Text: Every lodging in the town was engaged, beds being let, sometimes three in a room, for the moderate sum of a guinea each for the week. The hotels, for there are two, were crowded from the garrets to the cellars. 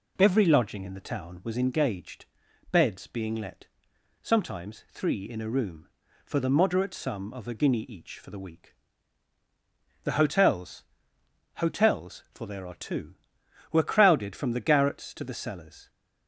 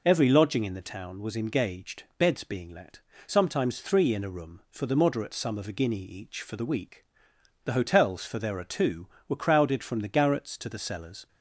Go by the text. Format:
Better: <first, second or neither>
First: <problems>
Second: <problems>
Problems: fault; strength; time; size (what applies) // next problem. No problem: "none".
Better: second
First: says "hotels" twice; at 11.5 s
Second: none